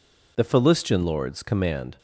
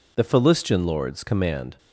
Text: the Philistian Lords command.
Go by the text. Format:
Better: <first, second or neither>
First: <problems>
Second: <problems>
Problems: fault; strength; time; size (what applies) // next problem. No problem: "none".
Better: neither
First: none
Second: none